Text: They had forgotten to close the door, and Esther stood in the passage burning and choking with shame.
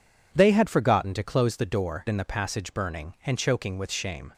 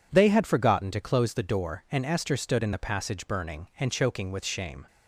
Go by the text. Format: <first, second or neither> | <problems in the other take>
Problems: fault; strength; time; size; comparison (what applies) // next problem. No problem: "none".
second | skips "and Esther stood"; at 2.0 s